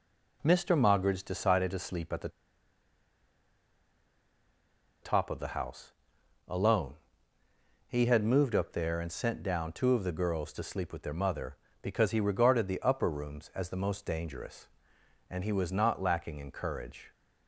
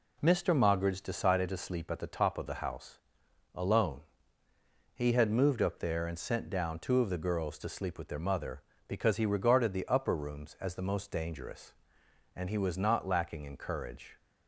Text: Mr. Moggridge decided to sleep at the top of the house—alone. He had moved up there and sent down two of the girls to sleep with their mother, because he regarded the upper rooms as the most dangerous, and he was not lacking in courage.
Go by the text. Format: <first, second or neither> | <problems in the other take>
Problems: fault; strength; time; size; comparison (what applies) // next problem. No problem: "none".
second | pauses between "the" and "top"; strong; at 2.2 s; 2.7 s long